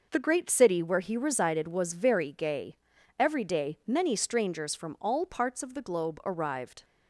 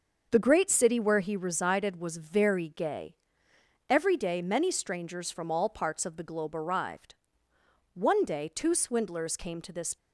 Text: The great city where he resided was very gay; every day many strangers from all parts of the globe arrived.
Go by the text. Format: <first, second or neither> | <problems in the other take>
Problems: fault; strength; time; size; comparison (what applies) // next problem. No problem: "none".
first | starts louder than the rest; until 1.3 s; 6 dB // goes on to say "One day two swindlers came to this"; strong; from 7.9 s on; 2.0 s long